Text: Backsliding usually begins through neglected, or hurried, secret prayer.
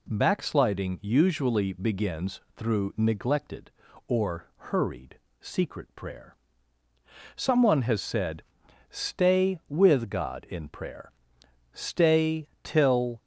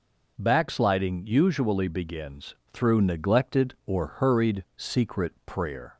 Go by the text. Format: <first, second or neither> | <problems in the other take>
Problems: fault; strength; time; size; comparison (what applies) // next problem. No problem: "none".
second | pauses between "begins" and "through"; slight; at 2.3 s; 0.16 s long; slight in the second // goes on to say "Someone has said Stay with God in prayer stay till"; strong; from 7.3 s on; 5.8 s long